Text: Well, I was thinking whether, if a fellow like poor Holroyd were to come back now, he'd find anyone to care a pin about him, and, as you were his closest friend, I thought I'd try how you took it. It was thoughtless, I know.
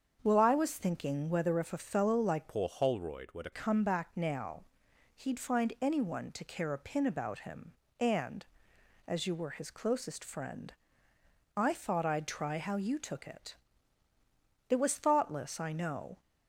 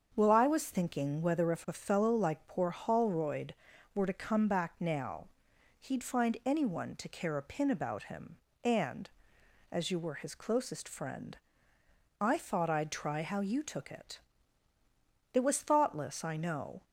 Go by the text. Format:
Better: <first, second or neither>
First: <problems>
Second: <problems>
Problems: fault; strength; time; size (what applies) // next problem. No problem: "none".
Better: second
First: starts louder than the rest; until 1.2 s; 7 dB // changes voice from "poor" to "to"; from 2.4 to 3.4 s; 1.0 s long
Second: starts louder than the rest; until 1.1 s; 7 dB